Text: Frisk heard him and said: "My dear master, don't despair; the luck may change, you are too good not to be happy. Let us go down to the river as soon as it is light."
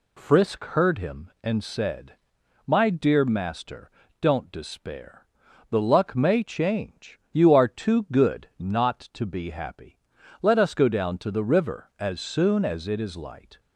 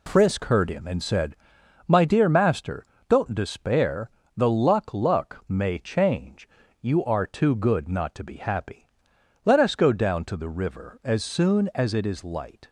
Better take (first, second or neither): first